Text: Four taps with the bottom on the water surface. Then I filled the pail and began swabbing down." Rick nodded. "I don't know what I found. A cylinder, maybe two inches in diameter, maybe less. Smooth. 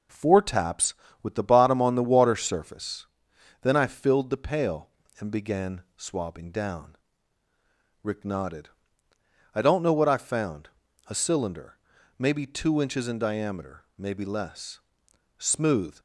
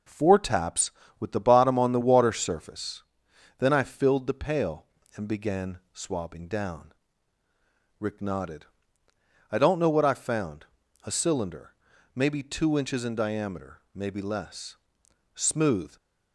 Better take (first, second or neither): neither